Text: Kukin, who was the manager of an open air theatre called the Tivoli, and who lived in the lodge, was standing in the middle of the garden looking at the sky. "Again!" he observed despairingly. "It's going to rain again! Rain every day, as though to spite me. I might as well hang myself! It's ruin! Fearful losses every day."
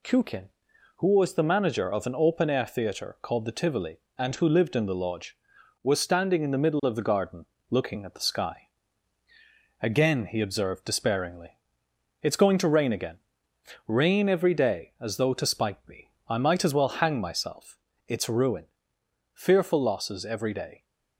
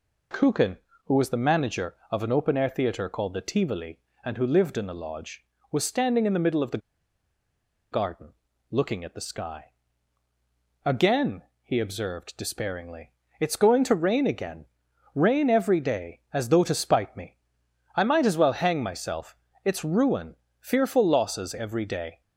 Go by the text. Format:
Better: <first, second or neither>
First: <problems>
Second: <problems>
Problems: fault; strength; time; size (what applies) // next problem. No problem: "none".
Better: first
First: pauses between "garden" and "looking"; slight; at 7.4 s; 0.24 s long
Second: pauses between "the" and "garden"; at 6.7 s; 1.1 s long // pauses between "garden" and "looking"; at 8.2 s; 0.42 s long